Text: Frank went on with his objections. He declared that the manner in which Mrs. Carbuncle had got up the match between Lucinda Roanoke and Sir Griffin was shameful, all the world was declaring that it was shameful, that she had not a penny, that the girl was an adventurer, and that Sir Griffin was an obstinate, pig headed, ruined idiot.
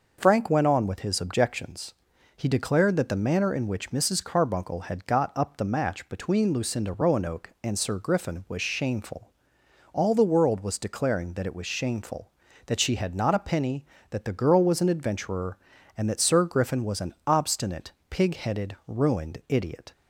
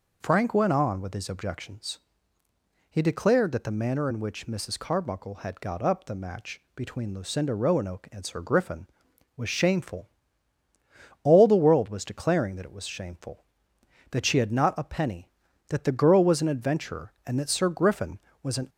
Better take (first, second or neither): first